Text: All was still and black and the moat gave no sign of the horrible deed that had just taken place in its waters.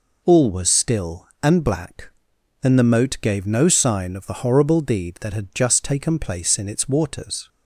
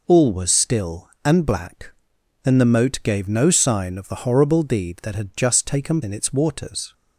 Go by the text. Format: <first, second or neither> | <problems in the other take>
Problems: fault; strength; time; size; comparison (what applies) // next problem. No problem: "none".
first | skips "place"; at 6.0 s